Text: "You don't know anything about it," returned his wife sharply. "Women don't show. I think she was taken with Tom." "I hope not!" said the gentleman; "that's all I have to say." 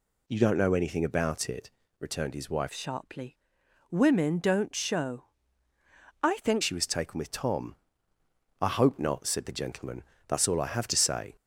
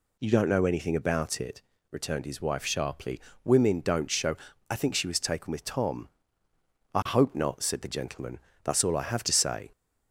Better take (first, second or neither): second